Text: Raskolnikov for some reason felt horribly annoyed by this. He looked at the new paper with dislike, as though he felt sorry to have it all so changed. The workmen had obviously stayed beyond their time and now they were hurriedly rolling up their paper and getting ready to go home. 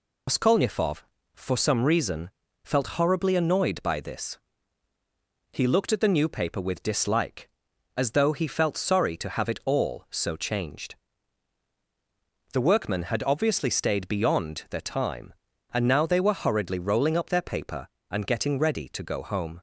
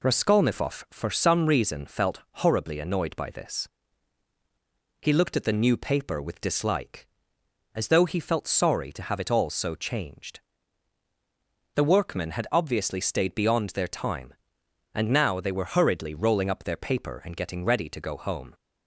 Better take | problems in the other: second | loses the start of "Raskolnikov"; at 0.2 s; 105 ms // pauses between "reason" and "felt"; slight; at 2.2 s; 0.34 s long

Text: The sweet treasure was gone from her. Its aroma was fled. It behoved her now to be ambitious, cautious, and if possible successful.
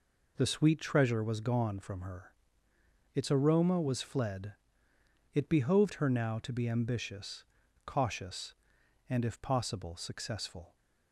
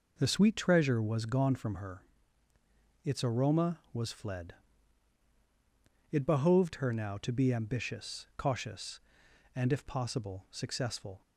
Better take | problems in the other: neither | none

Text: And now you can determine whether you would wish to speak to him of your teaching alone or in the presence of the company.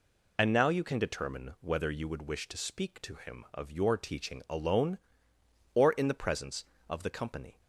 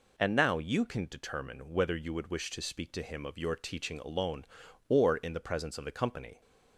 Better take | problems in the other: neither | none

